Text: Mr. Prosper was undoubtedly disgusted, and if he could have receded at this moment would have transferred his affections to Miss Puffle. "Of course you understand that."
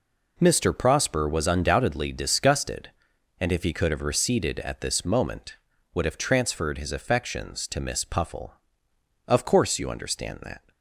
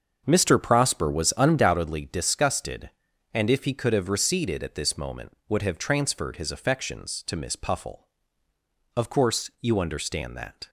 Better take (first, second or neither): first